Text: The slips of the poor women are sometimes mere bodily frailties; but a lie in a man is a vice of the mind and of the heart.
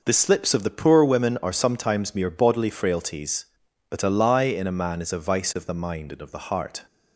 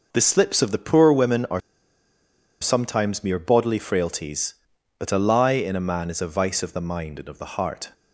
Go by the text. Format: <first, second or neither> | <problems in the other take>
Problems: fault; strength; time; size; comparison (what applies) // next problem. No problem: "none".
first | pauses between "are" and "sometimes"; at 1.6 s; 1.0 s long